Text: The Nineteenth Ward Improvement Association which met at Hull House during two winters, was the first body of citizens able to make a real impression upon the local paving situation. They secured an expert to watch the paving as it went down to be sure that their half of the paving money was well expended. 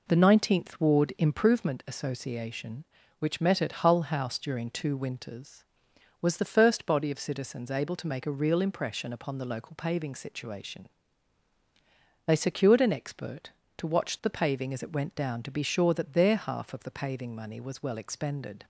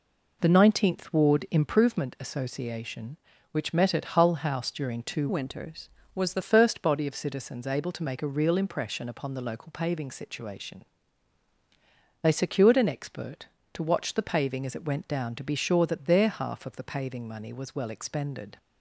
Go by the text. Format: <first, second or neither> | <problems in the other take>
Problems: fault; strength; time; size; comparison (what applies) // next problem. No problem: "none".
first | changes voice from "winters" to "the"; from 5.2 to 6.4 s; 1.2 s long